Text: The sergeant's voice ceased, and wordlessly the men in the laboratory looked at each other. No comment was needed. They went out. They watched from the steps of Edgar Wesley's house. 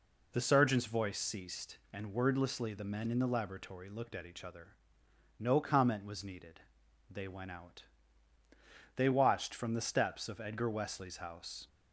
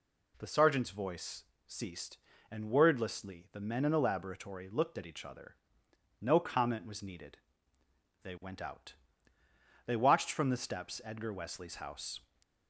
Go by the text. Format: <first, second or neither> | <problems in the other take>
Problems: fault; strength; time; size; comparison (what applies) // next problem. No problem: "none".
first | pauses between "voice" and "ceased"; slight; at 1.4 s; 0.22 s long // skips "of"; at 11.0 s